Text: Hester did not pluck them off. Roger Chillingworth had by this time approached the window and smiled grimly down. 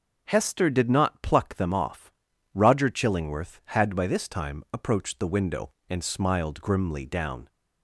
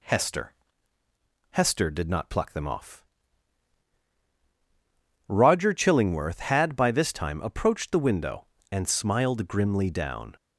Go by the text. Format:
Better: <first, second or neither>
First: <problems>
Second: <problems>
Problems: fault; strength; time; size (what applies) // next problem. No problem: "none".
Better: first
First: none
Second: says "Hester" twice; at 1.5 s